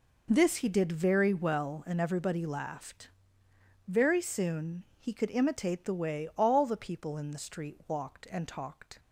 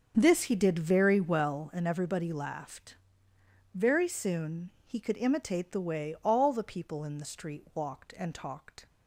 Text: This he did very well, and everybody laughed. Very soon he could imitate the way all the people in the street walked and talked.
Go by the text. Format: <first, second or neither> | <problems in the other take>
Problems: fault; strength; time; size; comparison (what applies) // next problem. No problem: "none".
first | starts louder than the rest; until 1.7 s; 6.5 dB // pauses between "soon" and "he"; slight; at 4.6 s; 0.16 s long; slight in the first